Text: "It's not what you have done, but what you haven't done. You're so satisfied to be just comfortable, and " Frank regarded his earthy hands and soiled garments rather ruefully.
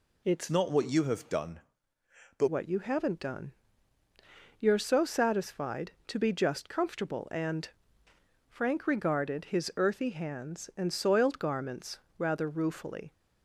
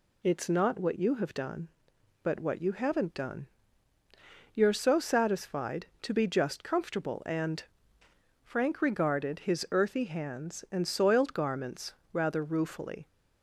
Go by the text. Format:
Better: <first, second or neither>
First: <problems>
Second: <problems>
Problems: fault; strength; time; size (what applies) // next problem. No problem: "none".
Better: second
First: changes voice from "not" to "but"; from 0.5 to 2.4 s; 1.9 s long // pauses between "garments" and "rather"; slight; at 11.9 s; 0.18 s long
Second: pauses between "garments" and "rather"; slight; at 11.9 s; 0.18 s long